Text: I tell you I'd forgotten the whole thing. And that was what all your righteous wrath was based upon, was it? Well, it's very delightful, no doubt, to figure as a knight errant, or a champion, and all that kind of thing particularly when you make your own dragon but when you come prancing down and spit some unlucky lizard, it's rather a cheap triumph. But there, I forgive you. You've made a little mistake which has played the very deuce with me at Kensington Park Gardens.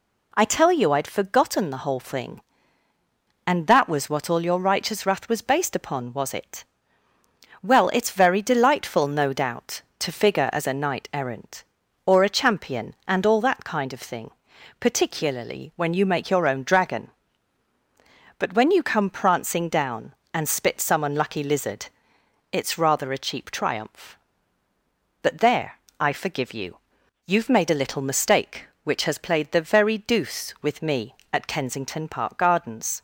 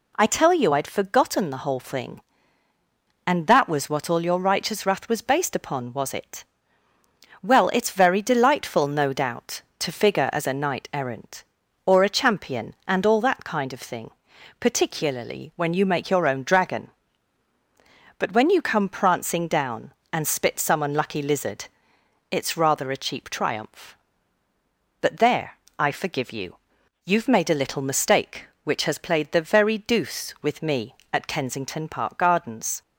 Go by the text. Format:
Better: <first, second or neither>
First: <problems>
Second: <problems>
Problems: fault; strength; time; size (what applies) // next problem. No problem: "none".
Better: neither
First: pauses between "thing" and "particularly"; noticeable; at 14.3 s; 0.48 s long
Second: pauses between "thing" and "particularly"; noticeable; at 14.1 s; 0.48 s long